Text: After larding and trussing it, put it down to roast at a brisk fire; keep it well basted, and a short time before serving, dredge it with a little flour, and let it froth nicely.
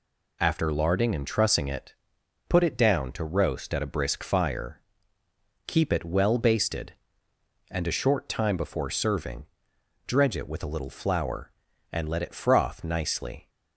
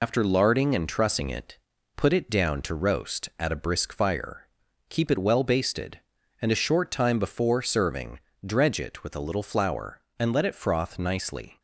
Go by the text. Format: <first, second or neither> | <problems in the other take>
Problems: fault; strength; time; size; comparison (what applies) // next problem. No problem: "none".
first | loses the start of "After"; at 0.0 s; 85 ms